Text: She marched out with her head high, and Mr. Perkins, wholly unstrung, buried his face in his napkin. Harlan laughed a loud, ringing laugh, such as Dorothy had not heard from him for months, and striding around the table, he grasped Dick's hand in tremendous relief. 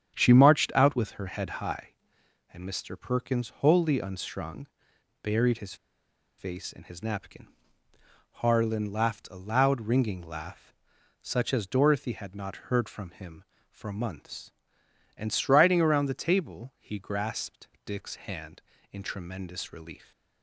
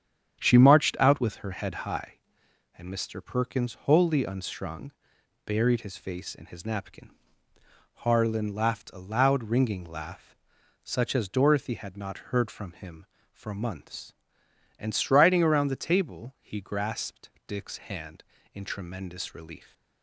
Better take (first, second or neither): second